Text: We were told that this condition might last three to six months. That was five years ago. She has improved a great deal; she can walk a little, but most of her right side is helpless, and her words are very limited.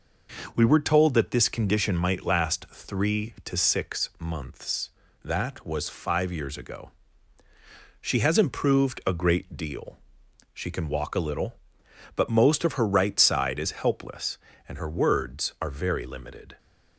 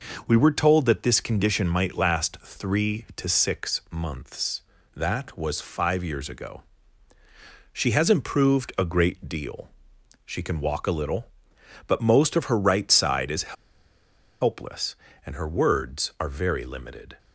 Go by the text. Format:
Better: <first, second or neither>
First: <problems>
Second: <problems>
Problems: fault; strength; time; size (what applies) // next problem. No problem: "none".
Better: first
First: none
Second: pauses between "is" and "helpless"; noticeable; at 13.5 s; 0.87 s long